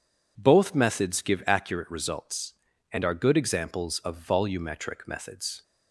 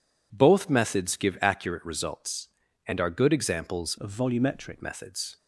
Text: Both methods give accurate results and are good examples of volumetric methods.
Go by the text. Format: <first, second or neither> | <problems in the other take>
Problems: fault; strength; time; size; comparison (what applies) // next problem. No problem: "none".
first | changes voice from "of" to "volumetric"; from 4.0 to 4.8 s; 0.8 s long